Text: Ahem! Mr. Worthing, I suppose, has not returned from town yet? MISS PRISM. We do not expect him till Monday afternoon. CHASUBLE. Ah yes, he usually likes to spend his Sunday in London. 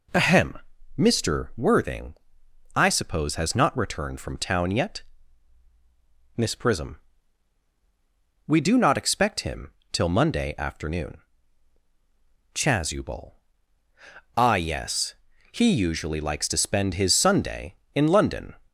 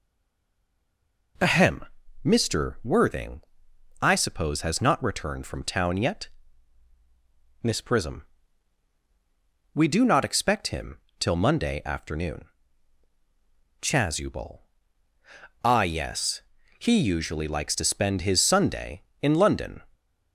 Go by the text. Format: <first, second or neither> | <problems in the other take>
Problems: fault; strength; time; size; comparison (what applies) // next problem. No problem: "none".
first | stays silent before the first word; noticeable; until 1.3 s; 1.3 s long // pauses between "him" and "till"; slight; at 10.9 s; 0.22 s long; slight in the first